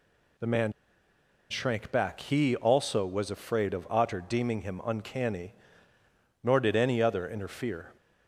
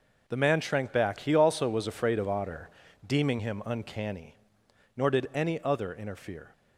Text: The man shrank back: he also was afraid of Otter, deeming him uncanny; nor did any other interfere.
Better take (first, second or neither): second